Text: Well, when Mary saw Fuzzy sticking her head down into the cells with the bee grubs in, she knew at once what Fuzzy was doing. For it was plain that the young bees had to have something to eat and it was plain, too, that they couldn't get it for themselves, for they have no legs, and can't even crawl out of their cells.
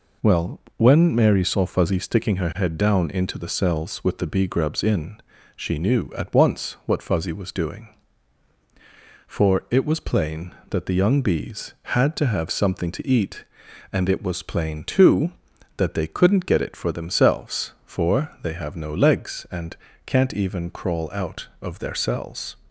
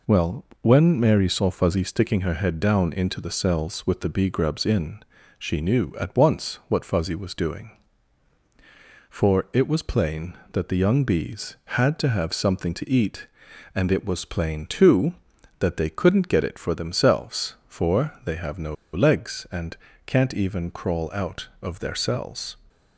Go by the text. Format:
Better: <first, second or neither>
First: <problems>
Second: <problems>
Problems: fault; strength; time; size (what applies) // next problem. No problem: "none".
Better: first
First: pauses between "and" and "can't"; slight; at 19.7 s; 0.28 s long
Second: pauses between "no" and "legs"; slight; at 18.7 s; 0.18 s long // pauses between "and" and "can't"; slight; at 19.7 s; 0.28 s long